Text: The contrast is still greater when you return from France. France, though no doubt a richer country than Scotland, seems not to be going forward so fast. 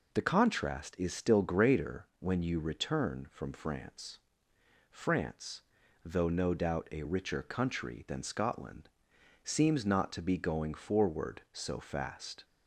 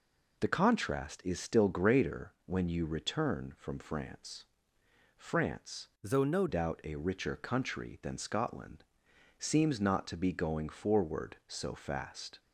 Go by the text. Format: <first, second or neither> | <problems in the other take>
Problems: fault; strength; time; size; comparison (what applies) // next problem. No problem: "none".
first | changes voice from "though" to "no"; from 6.0 to 6.4 s; 0.4 s long